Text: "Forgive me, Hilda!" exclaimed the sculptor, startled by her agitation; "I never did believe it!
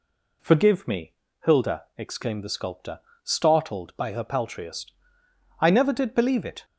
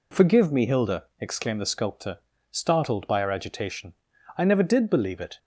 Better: second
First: says "paltriest" for "agitation"; at 4.2 s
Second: none

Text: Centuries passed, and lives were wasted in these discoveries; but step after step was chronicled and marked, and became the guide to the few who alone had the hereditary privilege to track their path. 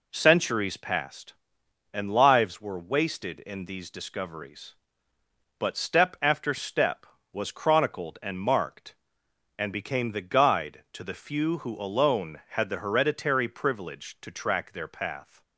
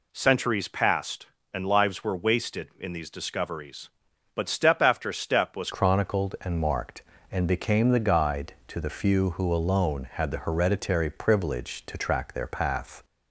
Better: first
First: none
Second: changes voice at "chronicled"; from 5.7 s on; 7.3 s long

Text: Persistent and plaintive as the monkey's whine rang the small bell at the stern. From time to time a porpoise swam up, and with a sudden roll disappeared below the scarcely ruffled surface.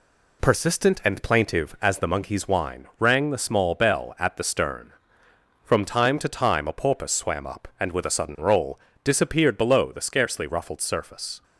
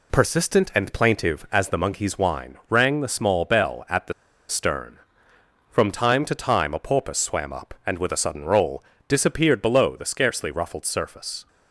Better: first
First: pauses between "roll" and "disappeared"; slight; at 8.7 s; 0.28 s long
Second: pauses between "the" and "stern"; slight; at 4.1 s; 0.36 s long // pauses between "roll" and "disappeared"; slight; at 8.8 s; 0.28 s long

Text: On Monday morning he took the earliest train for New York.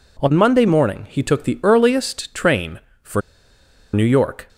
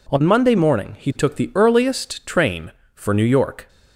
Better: second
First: pauses between "for" and "New"; noticeable; at 3.1 s; 0.73 s long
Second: none

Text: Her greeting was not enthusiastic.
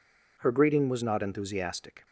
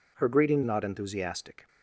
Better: first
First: none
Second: skips "was"; at 0.6 s

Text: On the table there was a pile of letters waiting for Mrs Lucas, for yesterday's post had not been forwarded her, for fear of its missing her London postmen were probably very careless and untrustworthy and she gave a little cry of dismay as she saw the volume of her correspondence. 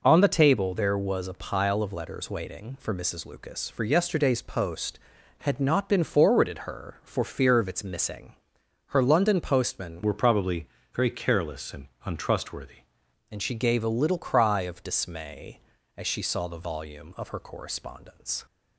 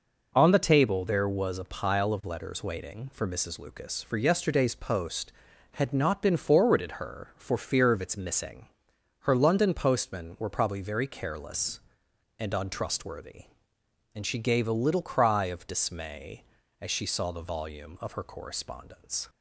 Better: second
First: pauses between "missing" and "her"; noticeable; at 8.3 s; 0.52 s long // changes voice from "were" to "untrustworthy"; from 10.0 to 12.8 s; 2.8 s long // pauses between "probably" and "very"; slight; at 10.6 s; 0.26 s long // pauses between "and" and "untrustworthy"; slight; at 11.8 s; 0.18 s long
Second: pauses between "missing" and "her"; noticeable; at 8.6 s; 0.52 s long

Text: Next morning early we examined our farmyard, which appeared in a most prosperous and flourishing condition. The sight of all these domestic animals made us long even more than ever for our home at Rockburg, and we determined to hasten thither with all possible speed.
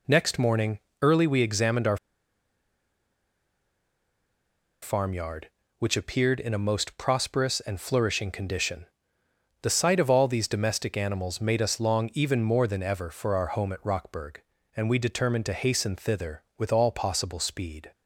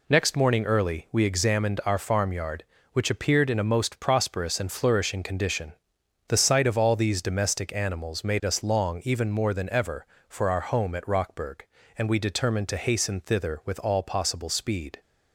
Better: second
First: pauses between "morning" and "early"; slight; at 0.7 s; 0.22 s long // pauses between "our" and "farmyard"; strong; at 1.9 s; 2.8 s long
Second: none

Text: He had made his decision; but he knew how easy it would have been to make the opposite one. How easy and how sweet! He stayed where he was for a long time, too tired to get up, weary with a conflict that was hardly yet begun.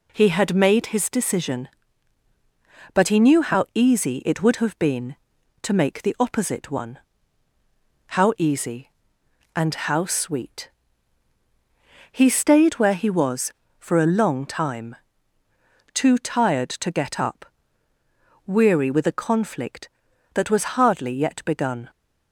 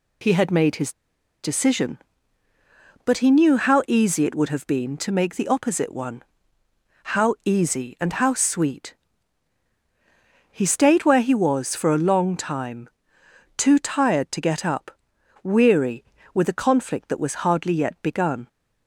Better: first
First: none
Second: pauses between "his" and "decision"; noticeable; at 0.9 s; 0.51 s long

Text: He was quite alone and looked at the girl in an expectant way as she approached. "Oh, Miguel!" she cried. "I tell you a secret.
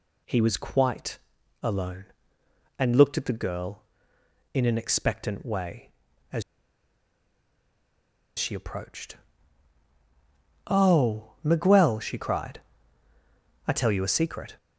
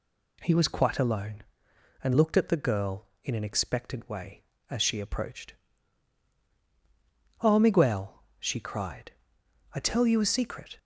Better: second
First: pauses between "quite" and "alone"; at 1.1 s; 0.44 s long // pauses between "as" and "she"; strong; at 6.4 s; 1.9 s long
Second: none

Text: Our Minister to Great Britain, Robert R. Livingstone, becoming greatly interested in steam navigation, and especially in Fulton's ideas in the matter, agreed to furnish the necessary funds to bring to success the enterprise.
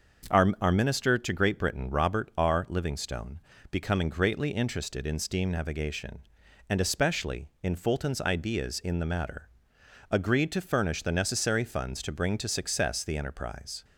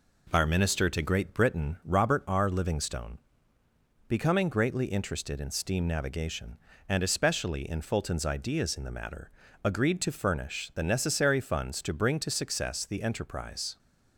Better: second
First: starts louder than the rest; until 1.4 s; 6.5 dB // says "Our" twice; at 0.6 s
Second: none

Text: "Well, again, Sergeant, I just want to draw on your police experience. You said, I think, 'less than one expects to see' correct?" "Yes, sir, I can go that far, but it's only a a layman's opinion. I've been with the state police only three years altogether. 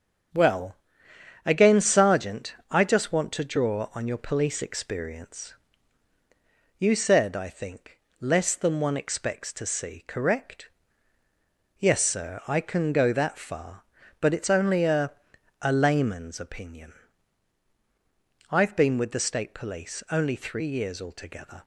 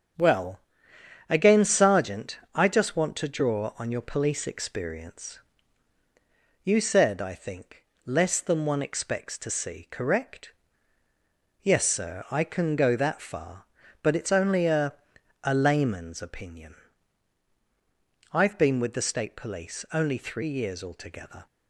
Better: neither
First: starts louder than the rest; strong; until 2.0 s; 8 dB // pauses between "a" and "a"; noticeable; at 15.1 s; 0.50 s long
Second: starts louder than the rest; strong; until 1.8 s; 7.5 dB // pauses between "a" and "a"; noticeable; at 14.9 s; 0.50 s long

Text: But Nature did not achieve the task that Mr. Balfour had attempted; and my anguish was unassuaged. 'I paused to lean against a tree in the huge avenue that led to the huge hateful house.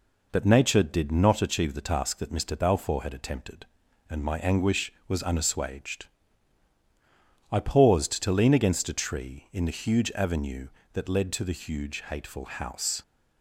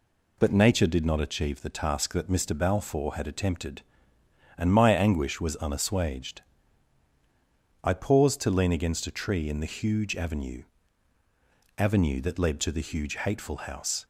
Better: first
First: none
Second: says "avenue" twice; at 11.7 s

